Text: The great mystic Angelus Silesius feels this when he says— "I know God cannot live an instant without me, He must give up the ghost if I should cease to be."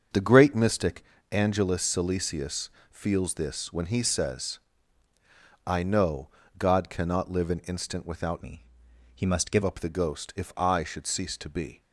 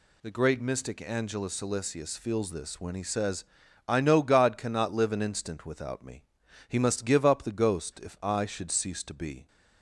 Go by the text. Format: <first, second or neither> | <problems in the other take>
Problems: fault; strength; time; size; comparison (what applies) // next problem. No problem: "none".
second | starts louder than the rest; until 1.4 s; 7 dB // pauses between "mystic" and "Angelus"; slight; at 1.0 s; 0.28 s long // pauses between "Silesius" and "feels"; slight; at 2.6 s; 0.22 s long // pauses between "know" and "God"; slight; at 6.2 s; 0.30 s long // changes voice from "me" to "give"; from 8.4 to 9.6 s; 1.2 s long